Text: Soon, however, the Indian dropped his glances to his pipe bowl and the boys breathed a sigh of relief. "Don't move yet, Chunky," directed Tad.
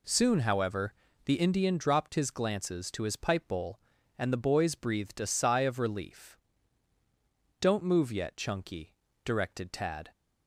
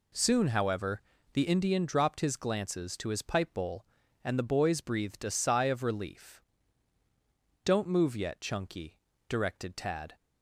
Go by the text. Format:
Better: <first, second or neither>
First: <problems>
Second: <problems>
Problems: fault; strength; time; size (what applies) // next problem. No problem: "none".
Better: neither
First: none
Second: none